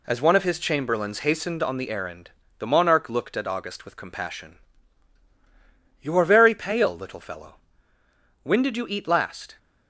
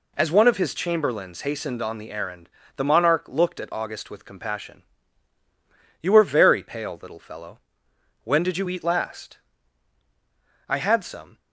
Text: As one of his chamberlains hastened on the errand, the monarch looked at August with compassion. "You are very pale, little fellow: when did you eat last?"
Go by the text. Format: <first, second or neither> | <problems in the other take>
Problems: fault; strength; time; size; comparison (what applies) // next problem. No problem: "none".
first | goes on to say "I had some"; noticeable; from 10.6 s on; 0.70 s long